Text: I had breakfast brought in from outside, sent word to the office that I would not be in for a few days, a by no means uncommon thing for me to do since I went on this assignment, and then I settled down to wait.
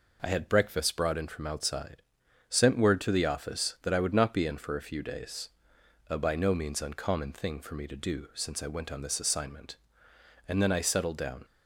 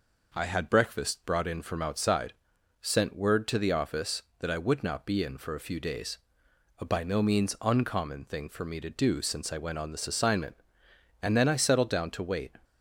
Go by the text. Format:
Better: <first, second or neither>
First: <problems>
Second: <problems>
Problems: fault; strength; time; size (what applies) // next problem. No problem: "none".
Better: second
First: stops before "to wait"; at 11.4 s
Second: none